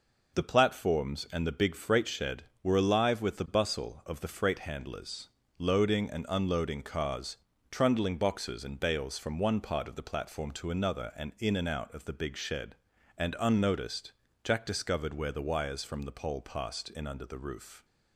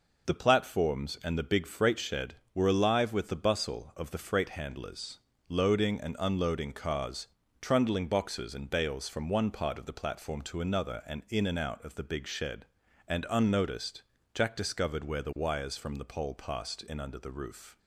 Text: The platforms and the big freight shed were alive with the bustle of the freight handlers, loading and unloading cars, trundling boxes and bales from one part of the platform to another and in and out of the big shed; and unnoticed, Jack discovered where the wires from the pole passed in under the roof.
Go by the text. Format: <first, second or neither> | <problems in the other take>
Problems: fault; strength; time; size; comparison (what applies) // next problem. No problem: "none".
neither | none